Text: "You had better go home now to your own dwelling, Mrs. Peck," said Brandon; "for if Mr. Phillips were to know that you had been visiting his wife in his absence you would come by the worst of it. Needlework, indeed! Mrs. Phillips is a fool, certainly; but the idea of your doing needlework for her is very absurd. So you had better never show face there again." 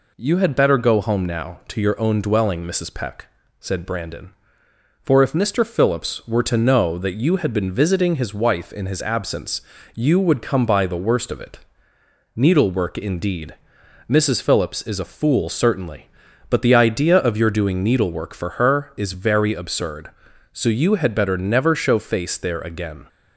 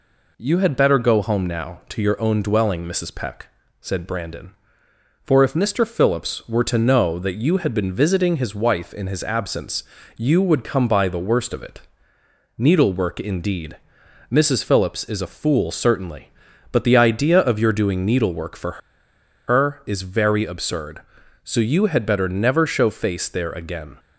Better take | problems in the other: first | pauses between "absence" and "you"; slight; at 9.8 s; 0.32 s long; slight in the first // pauses between "for" and "her"; noticeable; at 18.8 s; 0.69 s long

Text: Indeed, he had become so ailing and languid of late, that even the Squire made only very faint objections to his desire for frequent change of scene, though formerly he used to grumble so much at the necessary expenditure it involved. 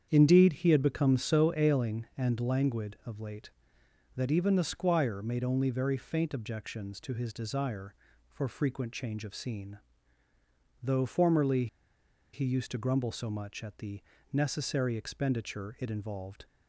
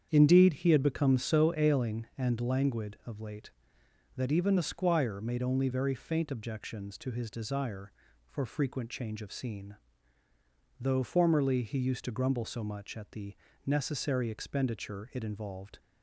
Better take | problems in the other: second | starts louder than the rest; strong; until 1.1 s; 8 dB; strong in the second // pauses between "formerly" and "he"; noticeable; at 11.6 s; 0.67 s long // pauses between "the" and "necessary"; slight; at 14.0 s; 0.32 s long; slight in the second

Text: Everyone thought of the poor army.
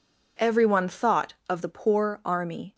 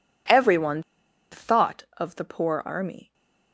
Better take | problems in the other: first | pauses between "Everyone" and "thought"; noticeable; at 0.8 s; 0.48 s long // stays silent after the last word; slight; from 3.0 s on; 0.5 s long

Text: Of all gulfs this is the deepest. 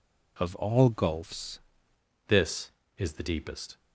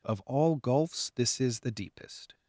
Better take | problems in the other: second | changes voice at "this"; from 2.2 s on; 1.5 s long

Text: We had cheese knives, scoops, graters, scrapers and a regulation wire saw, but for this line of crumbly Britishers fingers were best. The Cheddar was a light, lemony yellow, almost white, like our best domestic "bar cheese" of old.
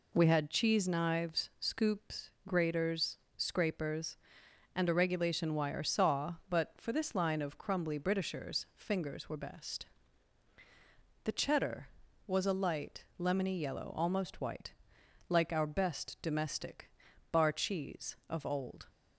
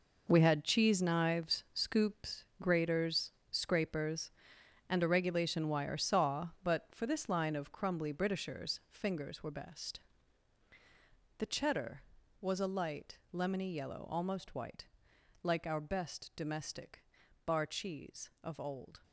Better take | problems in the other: first | gets quieter; strong; throughout; 11 dB // pauses between "domestic" and "bar"; at 17.0 s; 0.42 s long; also in the first

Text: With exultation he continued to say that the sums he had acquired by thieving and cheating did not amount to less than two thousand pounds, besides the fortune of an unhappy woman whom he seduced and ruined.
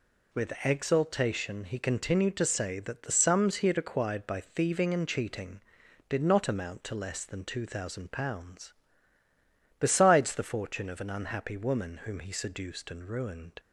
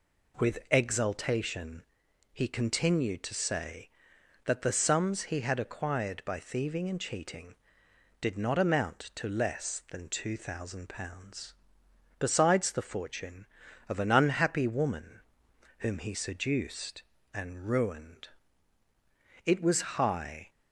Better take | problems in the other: first | pauses between "exultation" and "he"; noticeable; at 1.8 s; 0.50 s long // pauses between "woman" and "whom"; noticeable; at 15.2 s; 0.58 s long // goes on to say "It was high"; noticeable; from 19.4 s on; 1.0 s long

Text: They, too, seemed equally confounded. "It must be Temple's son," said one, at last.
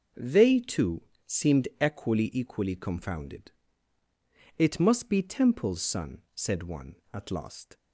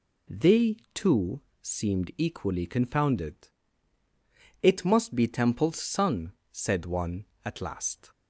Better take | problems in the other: second | says "equally" twice; at 2.3 s

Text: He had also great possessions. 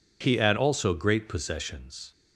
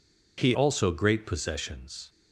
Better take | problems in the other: first | skips "had"; at 0.5 s

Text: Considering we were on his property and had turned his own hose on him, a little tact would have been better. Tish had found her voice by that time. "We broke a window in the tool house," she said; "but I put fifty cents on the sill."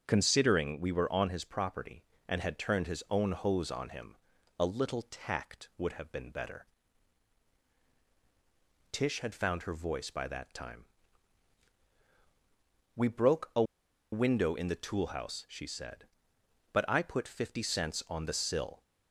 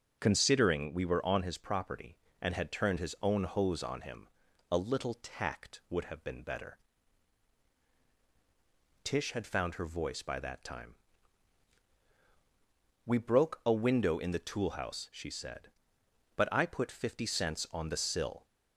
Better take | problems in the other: second | starts louder than the rest; strong; until 1.0 s; 7 dB; noticeable in the second // pauses between "a" and "window"; noticeable; at 13.6 s; 0.49 s long

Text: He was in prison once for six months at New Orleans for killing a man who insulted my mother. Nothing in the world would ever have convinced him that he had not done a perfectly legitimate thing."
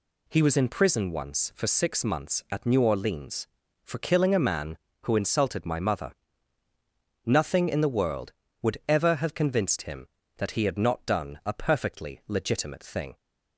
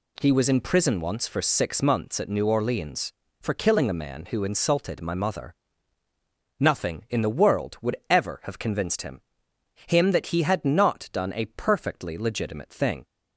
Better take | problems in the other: first | says "him" twice; at 9.8 s

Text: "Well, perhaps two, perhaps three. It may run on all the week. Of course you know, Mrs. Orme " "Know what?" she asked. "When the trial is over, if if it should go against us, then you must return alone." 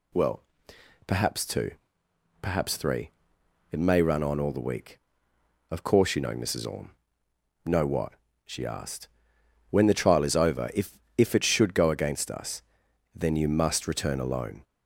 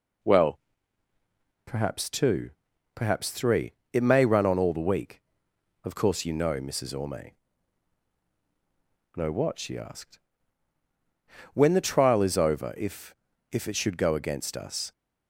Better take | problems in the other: first | pauses between "if" and "if"; slight; at 13.1 s; 0.36 s long; slight in the first // stops before "then you must return alone"; at 14.9 s

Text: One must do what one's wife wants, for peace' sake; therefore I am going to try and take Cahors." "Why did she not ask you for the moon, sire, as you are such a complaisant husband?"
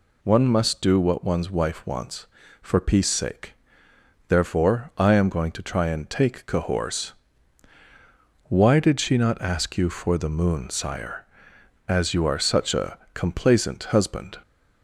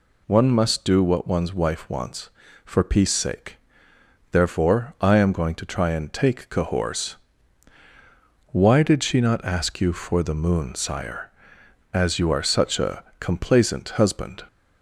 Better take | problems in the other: neither | pauses between "a" and "complaisant"; slight; the same in both

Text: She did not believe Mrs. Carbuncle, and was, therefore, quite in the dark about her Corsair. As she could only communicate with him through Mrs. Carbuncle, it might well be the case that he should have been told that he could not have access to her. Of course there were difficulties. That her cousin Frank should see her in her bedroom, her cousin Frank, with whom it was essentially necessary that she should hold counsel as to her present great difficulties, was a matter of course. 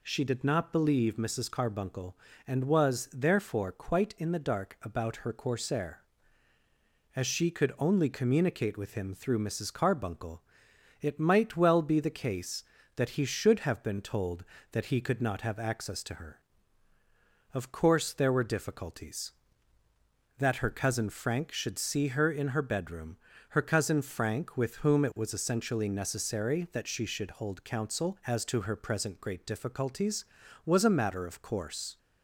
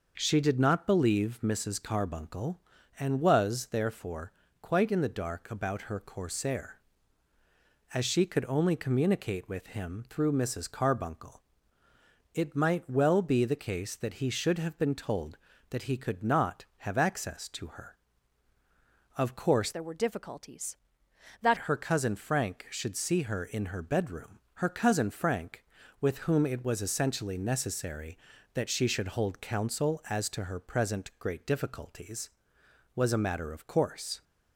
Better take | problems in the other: first | starts louder than the rest; noticeable; until 1.1 s; 6 dB // changes voice from "there" to "That"; from 19.7 to 21.5 s; 1.8 s long

